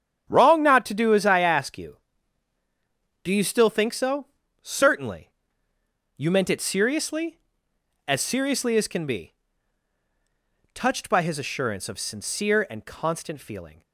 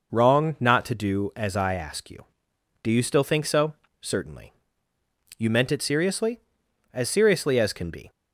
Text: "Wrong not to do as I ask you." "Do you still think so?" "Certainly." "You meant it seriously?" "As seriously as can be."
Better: second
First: starts louder than the rest; strong; until 1.2 s; 9 dB // goes on to say "Touched by his assurance of sincere and constant feeling"; strong; from 10.7 s on; 3.1 s long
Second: none

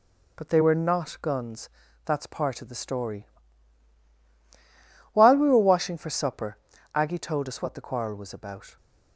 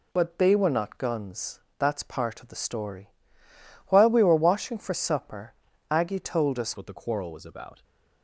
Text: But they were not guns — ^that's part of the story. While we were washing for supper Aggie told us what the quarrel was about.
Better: first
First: pauses between "supper" and "Aggie"; at 6.5 s; 0.38 s long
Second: pauses between "supper" and "Aggie"; slight; at 5.5 s; 0.36 s long // changes voice at "what"; from 6.7 s on; 1.1 s long

